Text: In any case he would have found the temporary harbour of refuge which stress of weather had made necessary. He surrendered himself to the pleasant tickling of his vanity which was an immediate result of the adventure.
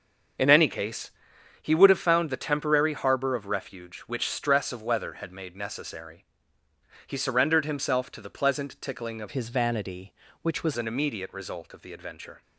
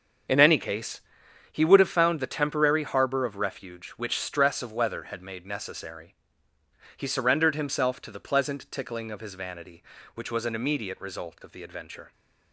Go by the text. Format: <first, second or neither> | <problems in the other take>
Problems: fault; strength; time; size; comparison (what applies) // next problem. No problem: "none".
second | starts louder than the rest; until 1.8 s; 6.5 dB; also in the second // pauses between "case" and "he"; noticeable; at 1.1 s; 0.50 s long; noticeable in the second // changes voice from "his" to "was"; from 9.3 to 10.7 s; 1.4 s long